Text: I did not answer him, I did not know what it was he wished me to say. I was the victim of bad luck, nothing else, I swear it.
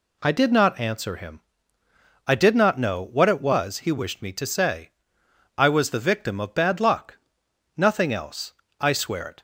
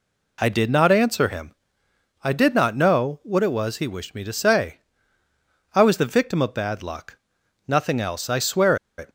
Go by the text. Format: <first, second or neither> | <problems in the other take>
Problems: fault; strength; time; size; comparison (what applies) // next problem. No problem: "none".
first | pauses between "swear" and "it"; slight; at 8.7 s; 0.20 s long